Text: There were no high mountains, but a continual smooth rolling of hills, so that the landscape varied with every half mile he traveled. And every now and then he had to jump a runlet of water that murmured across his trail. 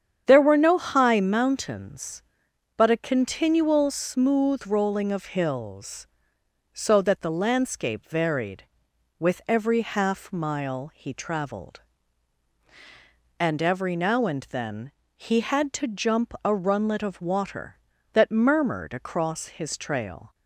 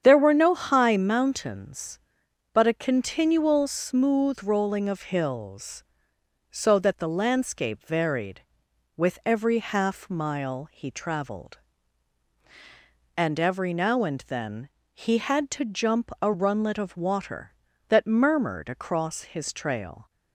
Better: neither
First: starts louder than the rest; strong; until 1.2 s; 8.5 dB // pauses between "then" and "he"; slight; at 14.9 s; 0.22 s long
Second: starts louder than the rest; strong; until 1.0 s; 8.5 dB // pauses between "then" and "he"; slight; at 14.6 s; 0.22 s long

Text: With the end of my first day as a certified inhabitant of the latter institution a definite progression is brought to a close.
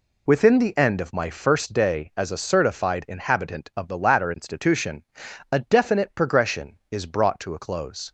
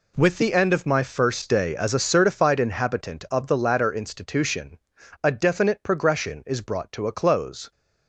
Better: second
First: says "Within" for "With"; at 0.2 s // pauses between "institution" and "a"; noticeable; at 5.0 s; 0.48 s long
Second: pauses between "institution" and "a"; noticeable; at 4.7 s; 0.46 s long

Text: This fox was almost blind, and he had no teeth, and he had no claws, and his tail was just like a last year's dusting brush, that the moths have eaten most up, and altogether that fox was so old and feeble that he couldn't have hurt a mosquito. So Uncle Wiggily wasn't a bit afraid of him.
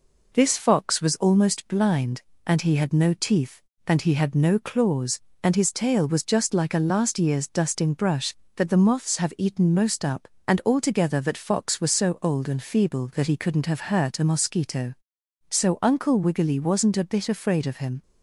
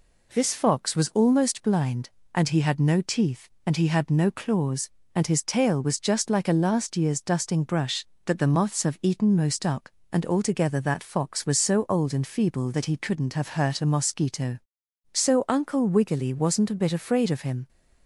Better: neither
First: none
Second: none

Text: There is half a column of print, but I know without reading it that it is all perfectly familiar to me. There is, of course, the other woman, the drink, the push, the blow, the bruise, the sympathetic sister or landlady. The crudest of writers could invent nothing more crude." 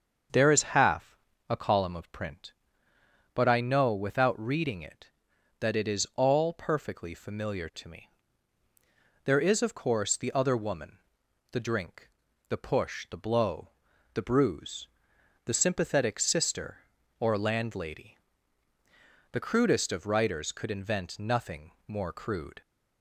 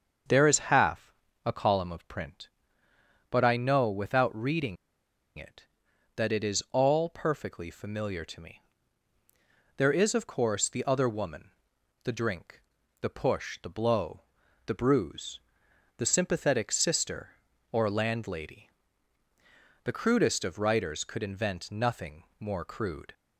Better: first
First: starts louder than the rest; until 1.6 s; 6.5 dB // pauses between "half" and "a"; slight; at 1.1 s; 0.32 s long // pauses between "nothing" and "more"; slight; at 21.7 s; 0.16 s long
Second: starts louder than the rest; until 1.6 s; 6.5 dB // pauses between "half" and "a"; slight; at 1.1 s; 0.32 s long // pauses between "reading" and "it"; noticeable; at 4.7 s; 0.61 s long // pauses between "nothing" and "more"; slight; at 22.2 s; 0.16 s long

